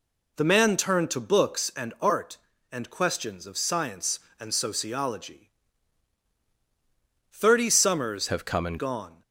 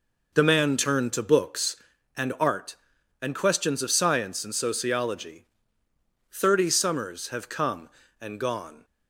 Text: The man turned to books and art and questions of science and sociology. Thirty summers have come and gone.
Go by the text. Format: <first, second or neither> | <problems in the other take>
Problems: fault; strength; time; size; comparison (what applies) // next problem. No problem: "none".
second | changes voice from "have" to "and"; from 8.2 to 8.7 s; 0.5 s long